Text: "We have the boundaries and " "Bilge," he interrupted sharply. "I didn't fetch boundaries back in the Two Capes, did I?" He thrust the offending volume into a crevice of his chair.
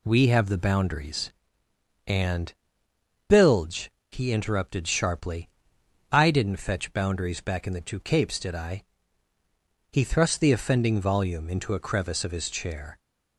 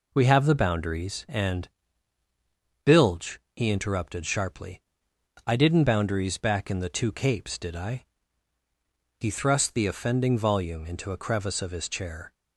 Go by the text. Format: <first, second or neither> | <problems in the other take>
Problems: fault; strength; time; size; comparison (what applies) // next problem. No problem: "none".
first | skips "fetch"; at 5.8 s